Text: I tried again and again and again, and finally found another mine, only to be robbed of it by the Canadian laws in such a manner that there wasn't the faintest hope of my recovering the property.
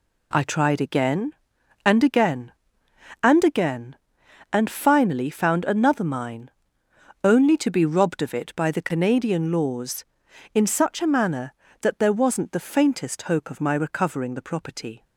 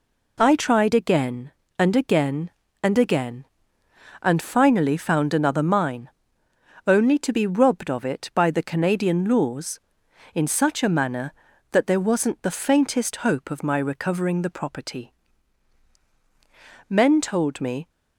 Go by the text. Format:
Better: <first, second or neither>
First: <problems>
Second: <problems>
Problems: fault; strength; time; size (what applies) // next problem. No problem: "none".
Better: first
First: none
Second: goes on to say "Men told me"; noticeable; from 16.8 s on; 1.0 s long